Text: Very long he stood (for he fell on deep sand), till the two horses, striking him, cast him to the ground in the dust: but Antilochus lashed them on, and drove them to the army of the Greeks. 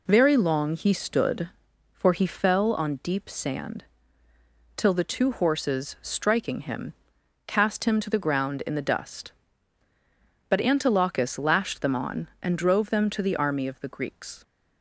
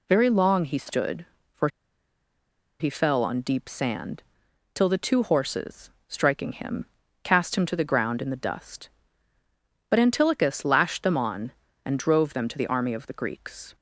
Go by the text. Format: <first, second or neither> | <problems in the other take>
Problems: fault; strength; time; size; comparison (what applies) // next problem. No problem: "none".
first | pauses between "for" and "he"; at 1.6 s; 1.1 s long